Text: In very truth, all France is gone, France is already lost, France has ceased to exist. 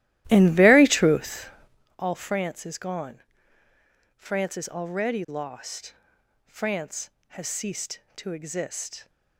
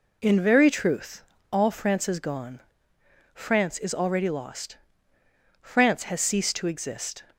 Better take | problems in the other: second | starts louder than the rest; strong; until 1.9 s; 14.5 dB

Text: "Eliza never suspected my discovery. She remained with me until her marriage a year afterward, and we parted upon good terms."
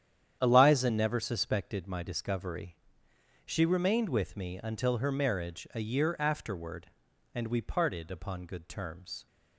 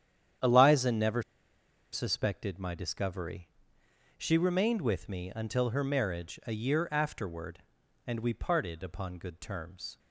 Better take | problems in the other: first | starts louder than the rest; strong; until 2.1 s; 9.5 dB; strong in the first // pauses between "never" and "suspected"; noticeable; at 1.2 s; 0.69 s long

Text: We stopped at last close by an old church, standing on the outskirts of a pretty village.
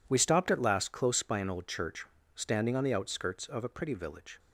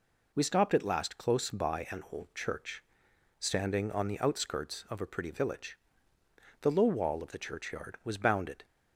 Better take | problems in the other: first | goes on to say "The low wall of the churchyard was bounded"; strong; from 6.6 s on; 2.0 s long

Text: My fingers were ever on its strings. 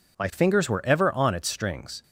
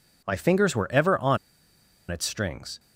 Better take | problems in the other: first | pauses between "on" and "its"; noticeable; at 1.3 s; 0.73 s long

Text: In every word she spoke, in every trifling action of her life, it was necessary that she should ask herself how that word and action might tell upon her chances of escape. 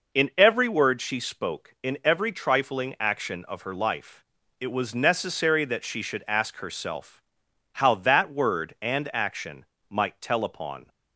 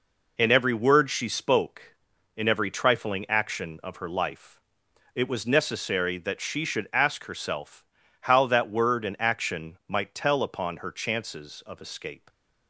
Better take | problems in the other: second | pauses between "herself" and "how"; noticeable; at 7.2 s; 0.52 s long; slight in the second // pauses between "action" and "might"; slight; at 9.6 s; 0.24 s long // stops before "her chances of escape"; at 10.8 s

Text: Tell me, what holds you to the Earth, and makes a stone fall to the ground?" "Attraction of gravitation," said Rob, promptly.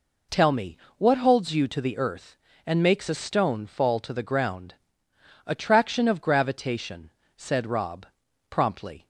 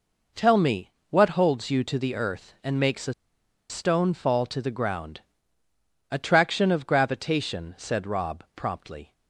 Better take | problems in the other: first | pauses between "a" and "stone"; noticeable; at 3.1 s; 0.56 s long

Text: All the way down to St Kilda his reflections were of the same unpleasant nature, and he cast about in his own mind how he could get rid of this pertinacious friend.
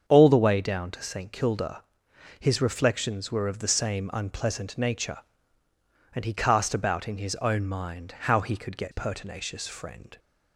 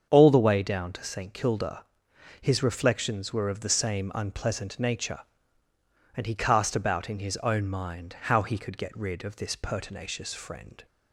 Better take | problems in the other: second | starts louder than the rest; until 1.0 s; 7 dB; also in the second // pauses between "Kilda" and "his"; noticeable; at 1.8 s; 0.56 s long; noticeable in the second // skips "rid of this"; at 8.9 s

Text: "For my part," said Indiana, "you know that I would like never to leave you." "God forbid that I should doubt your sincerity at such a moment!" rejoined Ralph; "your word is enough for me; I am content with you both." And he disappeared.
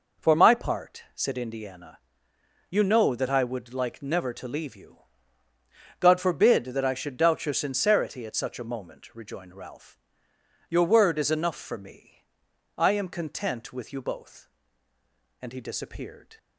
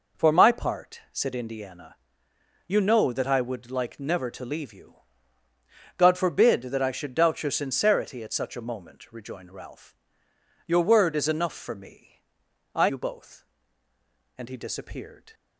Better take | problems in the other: first | skips "am content with"; at 12.8 s

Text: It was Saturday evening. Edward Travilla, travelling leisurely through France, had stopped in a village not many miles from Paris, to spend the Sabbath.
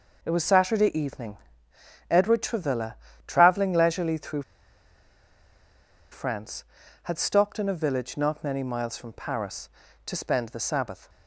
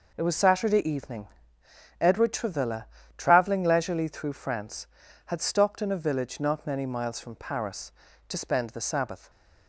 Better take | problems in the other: second | pauses between "through" and "France"; strong; at 4.4 s; 1.6 s long

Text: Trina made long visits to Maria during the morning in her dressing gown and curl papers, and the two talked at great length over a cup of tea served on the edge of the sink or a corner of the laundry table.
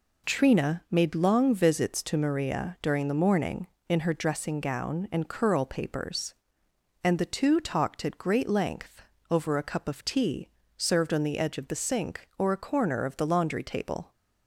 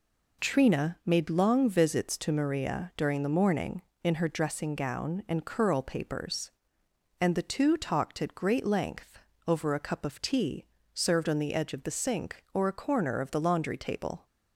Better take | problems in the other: neither | pauses between "length" and "over"; slight; the same in both // pauses between "tea" and "served"; slight; the same in both

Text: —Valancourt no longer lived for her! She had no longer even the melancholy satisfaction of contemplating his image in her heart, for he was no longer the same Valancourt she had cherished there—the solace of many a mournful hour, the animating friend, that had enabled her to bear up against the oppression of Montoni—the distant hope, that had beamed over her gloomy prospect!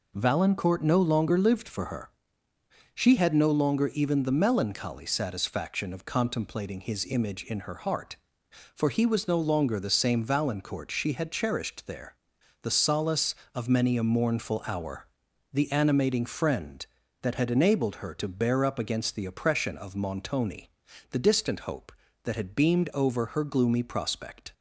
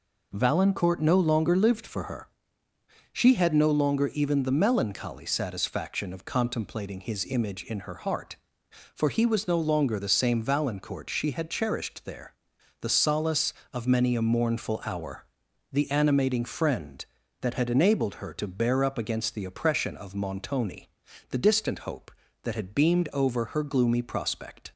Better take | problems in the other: neither | none

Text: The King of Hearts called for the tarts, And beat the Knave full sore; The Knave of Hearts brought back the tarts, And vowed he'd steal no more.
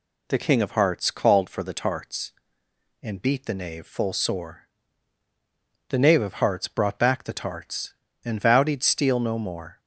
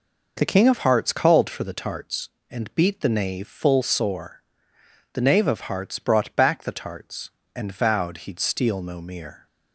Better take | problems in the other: first | says "mere" for "more"; at 9.0 s

